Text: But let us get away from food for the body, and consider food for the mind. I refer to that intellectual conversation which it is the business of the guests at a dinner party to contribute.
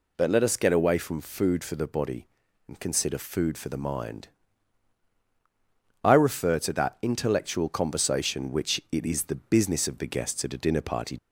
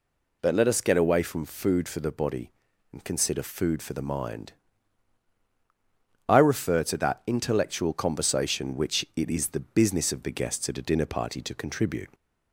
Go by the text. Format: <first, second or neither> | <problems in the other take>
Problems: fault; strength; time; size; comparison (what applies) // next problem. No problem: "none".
second | stops before "to contribute"; at 11.1 s